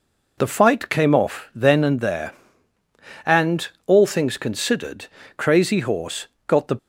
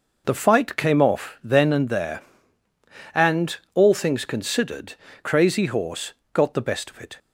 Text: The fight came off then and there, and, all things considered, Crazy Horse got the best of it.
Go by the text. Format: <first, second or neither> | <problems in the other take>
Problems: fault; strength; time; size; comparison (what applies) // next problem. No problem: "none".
second | pauses between "Horse" and "got"; slight; at 6.2 s; 0.18 s long; slight in the second // stops before "best of it"; at 6.7 s